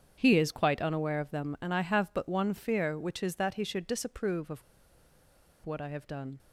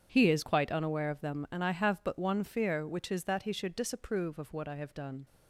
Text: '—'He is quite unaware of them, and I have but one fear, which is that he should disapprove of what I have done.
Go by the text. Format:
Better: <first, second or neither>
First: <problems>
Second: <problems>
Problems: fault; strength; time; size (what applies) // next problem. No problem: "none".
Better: second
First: starts louder than the rest; strong; until 1.1 s; 8 dB // pauses between "of" and "what"; at 4.6 s; 1.0 s long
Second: starts louder than the rest; strong; until 1.1 s; 8 dB